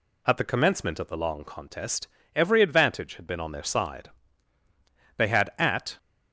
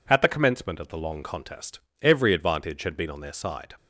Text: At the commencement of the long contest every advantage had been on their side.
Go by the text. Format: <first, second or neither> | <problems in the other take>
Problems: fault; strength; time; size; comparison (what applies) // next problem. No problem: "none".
second | pauses between "contest" and "every"; slight; at 2.0 s; 0.30 s long; slight in the second // goes on to say "They had at"; noticeable; from 5.1 s on; 0.80 s long